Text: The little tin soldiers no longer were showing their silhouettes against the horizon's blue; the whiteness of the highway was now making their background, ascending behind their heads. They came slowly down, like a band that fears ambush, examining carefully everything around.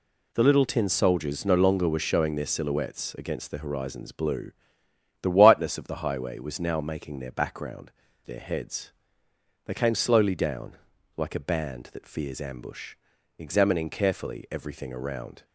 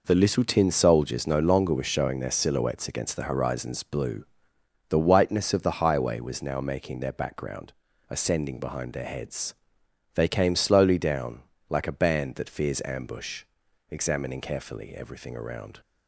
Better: second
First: skips "ascending behind"; at 8.0 s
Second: none

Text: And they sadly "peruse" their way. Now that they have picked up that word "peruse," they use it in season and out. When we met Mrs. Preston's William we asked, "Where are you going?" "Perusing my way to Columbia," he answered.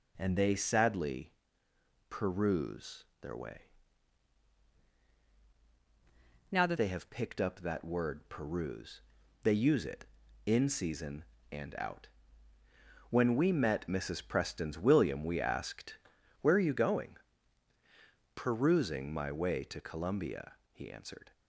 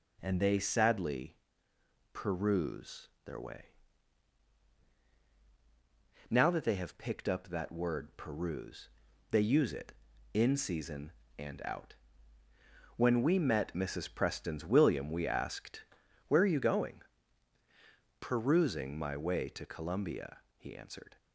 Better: second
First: pauses between "sadly" and "peruse"; noticeable; at 1.3 s; 0.76 s long // pauses between "peruse" and "their"; slight; at 3.0 s; 0.16 s long // changes voice from "Now" to "that"; from 6.4 to 6.7 s; 0.3 s long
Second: pauses between "sadly" and "peruse"; noticeable; at 1.3 s; 0.76 s long // pauses between "peruse" and "their"; slight; at 3.0 s; 0.16 s long

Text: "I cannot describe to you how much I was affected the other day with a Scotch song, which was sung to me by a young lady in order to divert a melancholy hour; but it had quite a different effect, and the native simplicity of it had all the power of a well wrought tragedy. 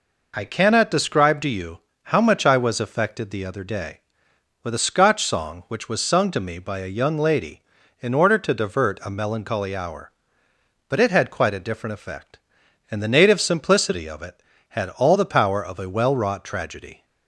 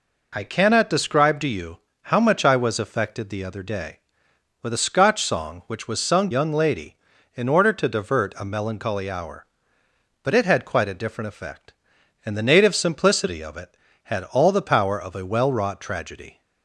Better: first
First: pauses between "you" and "how"; slight; at 1.7 s; 0.26 s long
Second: pauses between "you" and "how"; slight; at 1.7 s; 0.26 s long // skips "to me by a"; at 6.3 s

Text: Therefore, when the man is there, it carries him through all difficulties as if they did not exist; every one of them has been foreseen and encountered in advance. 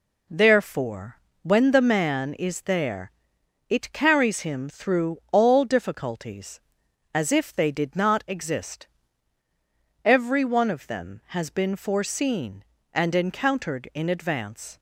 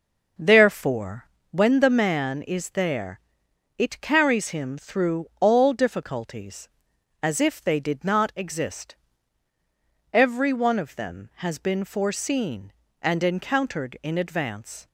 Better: first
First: none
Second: starts louder than the rest; noticeable; until 1.3 s; 5.5 dB

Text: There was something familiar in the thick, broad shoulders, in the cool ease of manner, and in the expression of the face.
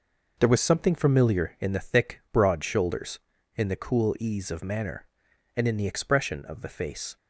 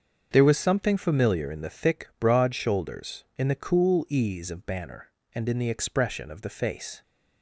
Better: first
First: none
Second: starts louder than the rest; until 1.3 s; 7 dB // says "banner" for "manner"; at 4.6 s

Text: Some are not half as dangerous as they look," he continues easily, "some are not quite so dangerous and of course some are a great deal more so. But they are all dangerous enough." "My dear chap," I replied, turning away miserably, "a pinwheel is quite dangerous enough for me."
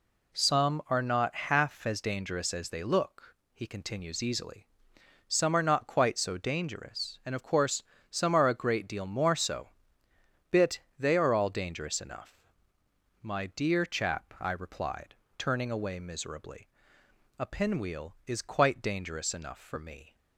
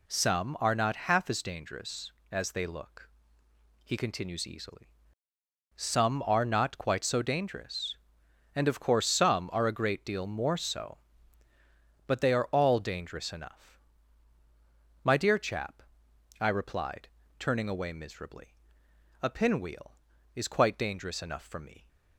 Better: second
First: pauses between "course" and "some"; slight; at 7.8 s; 0.28 s long // says "Bit" for "But"; at 10.4 s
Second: none

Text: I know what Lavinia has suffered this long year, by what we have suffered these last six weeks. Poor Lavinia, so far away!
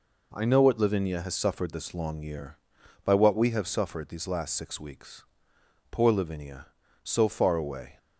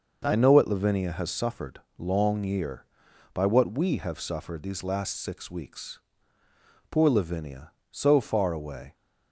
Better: first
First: none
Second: skips "this"; at 1.8 s

